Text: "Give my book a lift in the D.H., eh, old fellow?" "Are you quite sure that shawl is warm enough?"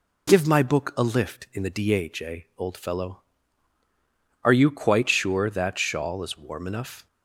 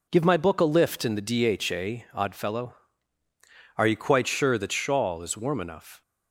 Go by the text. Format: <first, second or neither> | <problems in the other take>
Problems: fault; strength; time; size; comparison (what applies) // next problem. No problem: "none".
first | says "odd" for "old"; at 2.1 s